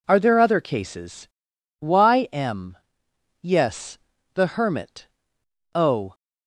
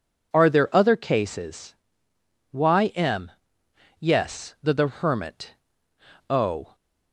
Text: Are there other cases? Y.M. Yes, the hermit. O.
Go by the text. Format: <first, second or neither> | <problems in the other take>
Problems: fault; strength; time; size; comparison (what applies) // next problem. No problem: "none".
first | says "the" twice; at 4.7 s